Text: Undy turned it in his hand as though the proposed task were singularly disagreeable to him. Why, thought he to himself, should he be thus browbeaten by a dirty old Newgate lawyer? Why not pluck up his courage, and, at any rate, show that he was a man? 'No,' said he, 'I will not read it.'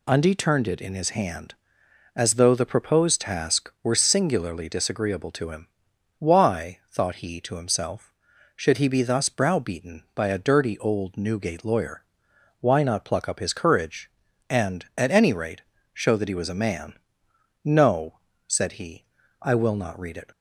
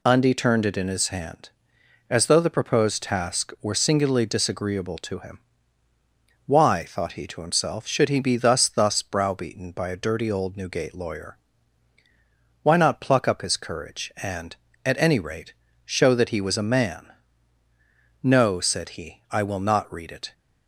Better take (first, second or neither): first